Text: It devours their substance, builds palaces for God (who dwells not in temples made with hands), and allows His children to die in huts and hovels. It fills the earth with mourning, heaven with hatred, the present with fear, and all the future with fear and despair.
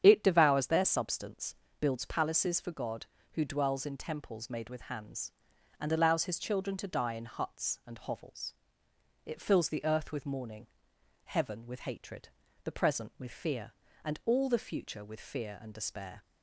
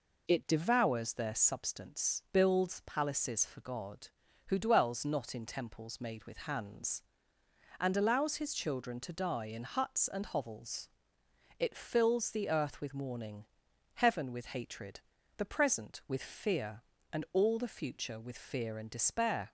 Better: second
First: starts louder than the rest; strong; until 1.0 s; 9 dB // skips "not"; at 3.8 s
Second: none

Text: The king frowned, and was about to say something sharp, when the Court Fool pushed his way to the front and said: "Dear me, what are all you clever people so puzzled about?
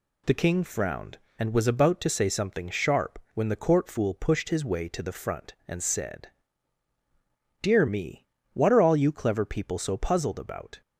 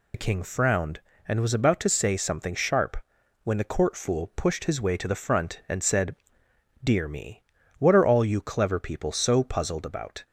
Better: first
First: none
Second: loses the start of "The"; at 0.1 s; 60 ms

